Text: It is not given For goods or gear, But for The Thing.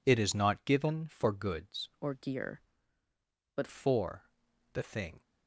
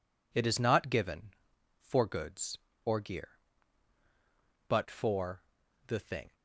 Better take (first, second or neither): second